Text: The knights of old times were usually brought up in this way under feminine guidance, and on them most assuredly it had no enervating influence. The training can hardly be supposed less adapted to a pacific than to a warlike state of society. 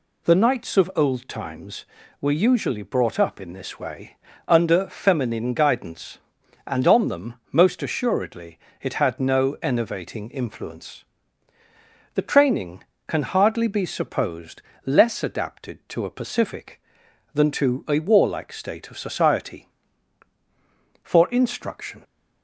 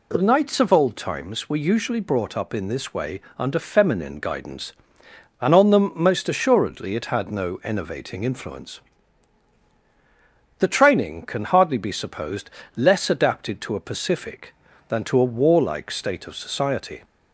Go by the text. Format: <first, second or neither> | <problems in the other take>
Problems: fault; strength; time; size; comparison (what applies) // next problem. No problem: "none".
second | pauses between "way" and "under"; slight; at 4.1 s; 0.30 s long; slight in the second // pauses between "them" and "most"; slight; at 7.3 s; 0.16 s long // pauses between "assuredly" and "it"; slight; at 8.5 s; 0.22 s long // pauses between "supposed" and "less"; slight; at 14.6 s; 0.24 s long; slight in the second // goes on to say "For instruction"; noticeable; from 21.0 s on; 1.0 s long